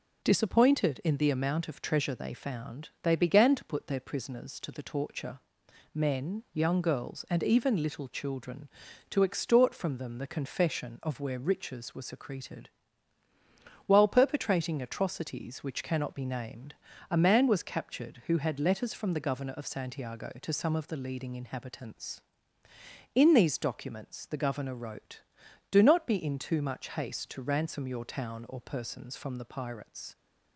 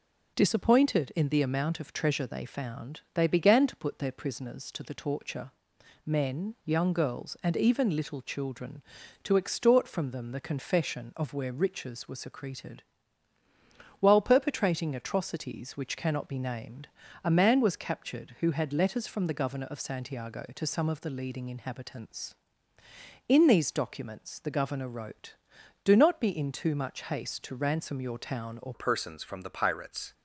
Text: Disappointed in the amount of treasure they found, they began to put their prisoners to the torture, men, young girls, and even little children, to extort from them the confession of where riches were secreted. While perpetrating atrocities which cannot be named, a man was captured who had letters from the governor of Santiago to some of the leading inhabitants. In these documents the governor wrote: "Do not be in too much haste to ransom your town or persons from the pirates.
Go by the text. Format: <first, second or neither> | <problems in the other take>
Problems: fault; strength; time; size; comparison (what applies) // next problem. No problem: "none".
first | changes voice at "persons"; from 28.7 s on; 1.4 s long